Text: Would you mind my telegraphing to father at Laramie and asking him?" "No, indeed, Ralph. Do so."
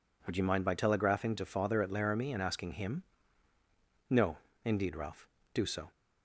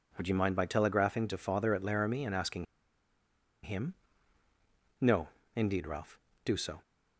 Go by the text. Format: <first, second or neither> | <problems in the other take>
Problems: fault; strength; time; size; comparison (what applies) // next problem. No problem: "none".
first | pauses between "asking" and "him"; at 2.6 s; 0.99 s long